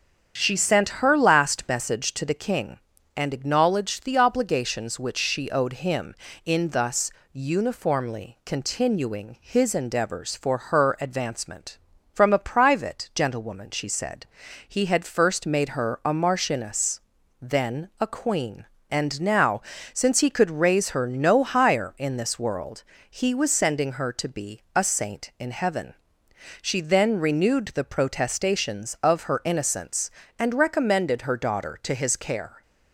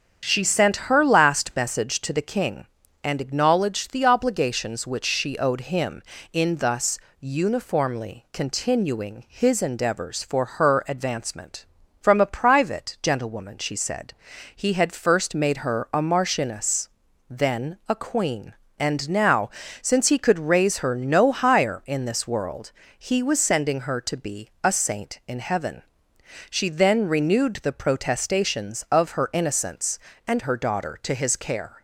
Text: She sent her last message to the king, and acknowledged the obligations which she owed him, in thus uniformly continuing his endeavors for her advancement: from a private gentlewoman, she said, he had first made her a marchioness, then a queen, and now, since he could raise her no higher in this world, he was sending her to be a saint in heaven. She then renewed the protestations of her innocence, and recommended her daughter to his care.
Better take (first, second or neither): first